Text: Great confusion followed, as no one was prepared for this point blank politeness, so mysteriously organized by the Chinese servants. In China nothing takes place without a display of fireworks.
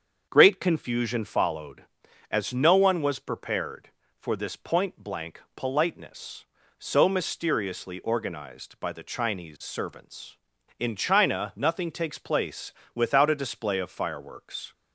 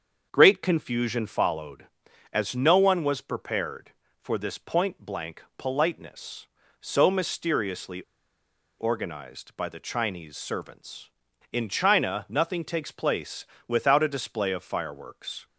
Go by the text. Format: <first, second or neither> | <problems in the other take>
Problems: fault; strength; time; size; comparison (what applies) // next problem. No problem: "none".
first | starts louder than the rest; until 1.3 s; 7 dB; also in the first // pauses between "mysteriously" and "organized"; noticeable; at 8.0 s; 0.77 s long // pauses between "place" and "without"; slight; at 13.4 s; 0.22 s long; slight in the first